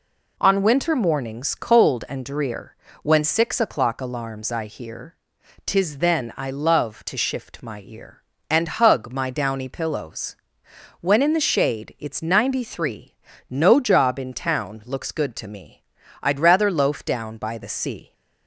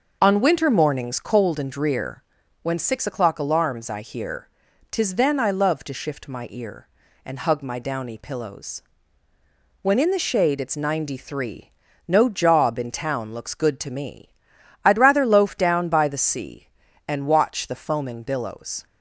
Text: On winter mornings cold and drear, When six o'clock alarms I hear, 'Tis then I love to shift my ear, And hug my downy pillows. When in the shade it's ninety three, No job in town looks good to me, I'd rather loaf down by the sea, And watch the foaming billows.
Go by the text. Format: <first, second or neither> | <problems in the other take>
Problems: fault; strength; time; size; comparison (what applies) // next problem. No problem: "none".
second | stops before "And watch the foaming billows"; at 18.1 s